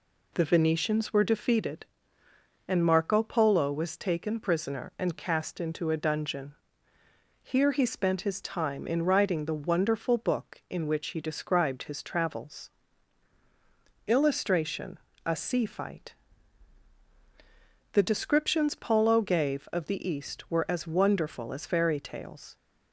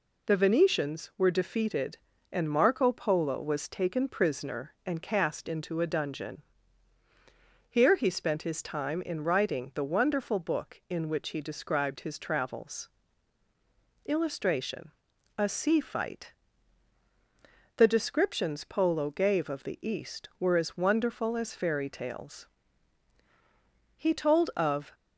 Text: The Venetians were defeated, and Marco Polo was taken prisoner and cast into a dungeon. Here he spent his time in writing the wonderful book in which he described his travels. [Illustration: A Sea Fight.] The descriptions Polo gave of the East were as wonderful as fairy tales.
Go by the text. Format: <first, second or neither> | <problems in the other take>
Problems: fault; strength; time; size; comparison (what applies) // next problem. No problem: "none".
first | goes on to say "He told of"; noticeable; from 23.9 s on; 0.96 s long